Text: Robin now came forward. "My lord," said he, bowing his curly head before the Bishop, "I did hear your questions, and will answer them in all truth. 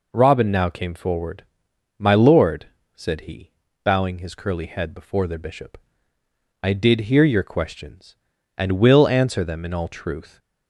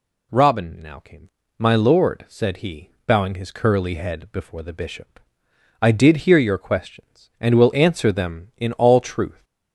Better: first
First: none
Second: skips "forward"; at 1.4 s

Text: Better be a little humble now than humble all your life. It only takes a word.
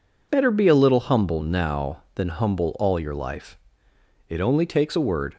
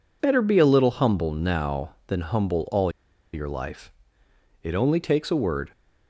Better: first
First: none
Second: pauses between "all" and "your"; at 2.9 s; 0.41 s long

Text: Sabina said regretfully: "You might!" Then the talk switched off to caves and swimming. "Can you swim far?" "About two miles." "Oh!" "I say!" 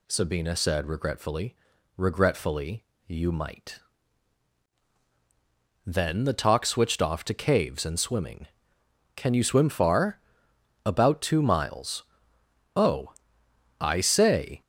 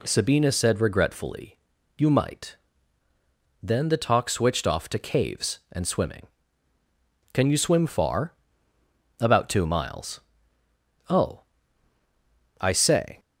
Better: second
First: says "regretfully" twice; at 1.9 s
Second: none

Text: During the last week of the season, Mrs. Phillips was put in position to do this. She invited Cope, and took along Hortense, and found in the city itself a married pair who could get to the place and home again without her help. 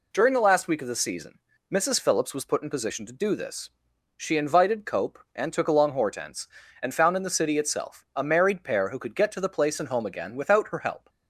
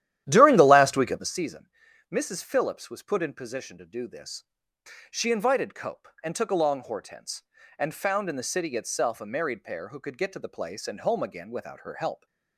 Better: first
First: none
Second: starts louder than the rest; strong; until 1.5 s; 12 dB

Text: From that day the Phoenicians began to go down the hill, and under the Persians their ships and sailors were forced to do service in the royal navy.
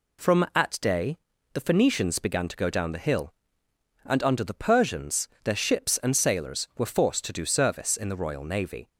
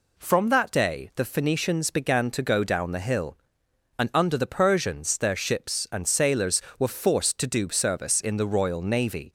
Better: second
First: says "at" for "that"; at 0.5 s // pauses between "day" and "the"; at 1.1 s; 0.38 s long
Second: none

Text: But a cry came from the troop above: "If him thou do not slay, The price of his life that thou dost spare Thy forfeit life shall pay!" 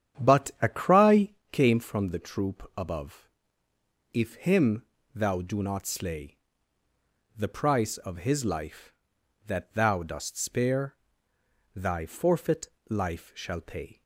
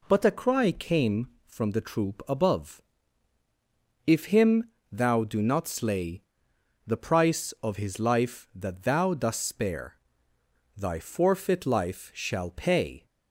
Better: second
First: starts louder than the rest; strong; until 1.5 s; 9 dB // pauses between "cry" and "came"; slight; at 1.2 s; 0.22 s long // pauses between "him" and "thou"; slight; at 4.8 s; 0.28 s long // pauses between "spare" and "Thy"; noticeable; at 10.9 s; 0.80 s long // pauses between "forfeit" and "life"; slight; at 12.6 s; 0.20 s long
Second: pauses between "him" and "thou"; slight; at 4.6 s; 0.22 s long // pauses between "spare" and "Thy"; noticeable; at 9.9 s; 0.80 s long

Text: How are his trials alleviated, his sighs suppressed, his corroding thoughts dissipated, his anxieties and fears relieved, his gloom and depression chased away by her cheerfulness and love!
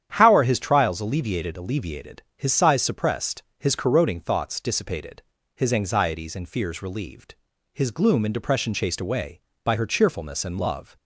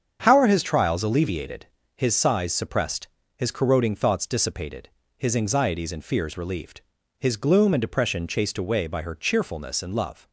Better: second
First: starts louder than the rest; strong; until 1.1 s; 9.5 dB // says "alleviated" twice; at 1.5 s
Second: starts louder than the rest; strong; until 1.2 s; 7.5 dB

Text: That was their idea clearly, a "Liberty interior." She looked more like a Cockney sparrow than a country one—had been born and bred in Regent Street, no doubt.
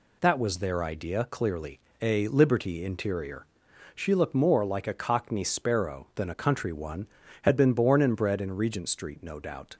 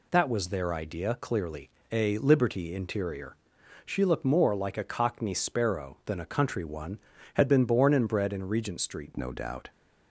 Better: first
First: none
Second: changes voice at "no"; from 9.1 s on; 0.5 s long

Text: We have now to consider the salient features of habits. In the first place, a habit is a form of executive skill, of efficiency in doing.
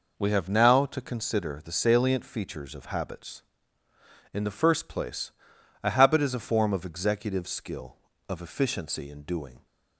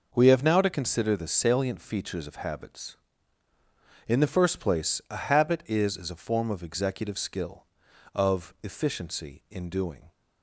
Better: first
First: none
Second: says "is" twice; at 5.9 s

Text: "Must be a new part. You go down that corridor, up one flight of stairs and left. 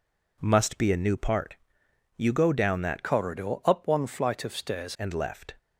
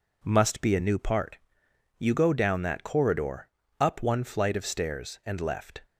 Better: second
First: changes voice from "corridor" to "stairs"; from 3.0 to 4.9 s; 1.9 s long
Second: none

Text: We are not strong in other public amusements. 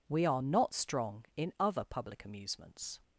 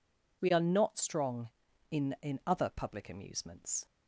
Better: first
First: none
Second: says "in" twice; at 2.2 s

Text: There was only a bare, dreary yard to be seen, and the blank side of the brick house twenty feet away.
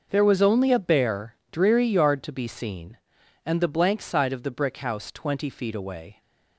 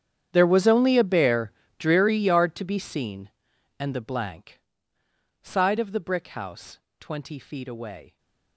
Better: first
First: none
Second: gets quieter; strong; throughout; 21 dB // pauses between "blank" and "side"; noticeable; at 4.5 s; 0.82 s long // pauses between "house" and "twenty"; slight; at 6.7 s; 0.20 s long

